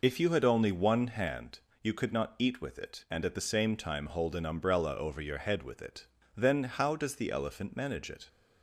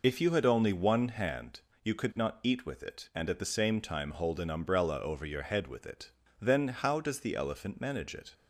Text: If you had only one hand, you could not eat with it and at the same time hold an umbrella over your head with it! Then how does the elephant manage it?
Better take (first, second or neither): neither